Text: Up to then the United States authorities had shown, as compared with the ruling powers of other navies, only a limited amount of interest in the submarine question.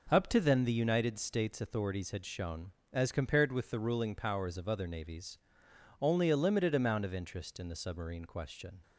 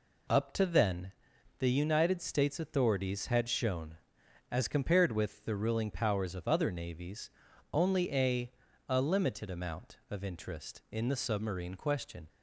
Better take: first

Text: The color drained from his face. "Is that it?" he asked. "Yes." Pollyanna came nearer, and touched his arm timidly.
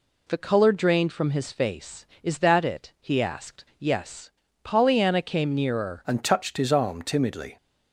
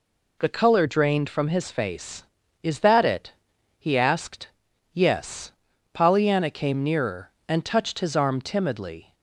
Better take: second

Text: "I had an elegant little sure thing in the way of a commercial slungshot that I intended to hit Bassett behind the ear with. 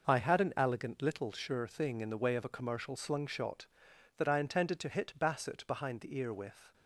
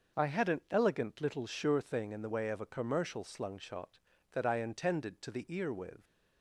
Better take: first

